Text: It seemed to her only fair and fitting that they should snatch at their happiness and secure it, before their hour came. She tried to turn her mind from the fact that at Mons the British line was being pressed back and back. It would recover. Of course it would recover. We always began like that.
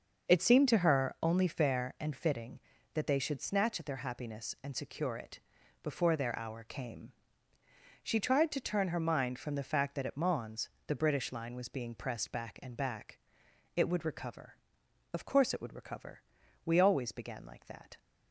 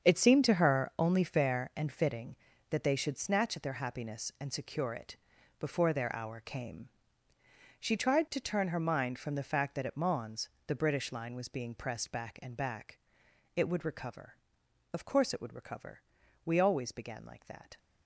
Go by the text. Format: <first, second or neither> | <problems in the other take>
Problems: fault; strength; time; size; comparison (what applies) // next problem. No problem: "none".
first | gets quieter; strong; throughout; 11.5 dB // starts louder than the rest; strong; until 1.1 s; 7.5 dB; noticeable in the first // pauses between "Mons" and "the"; slight; at 10.4 s; 0.20 s long; slight in the first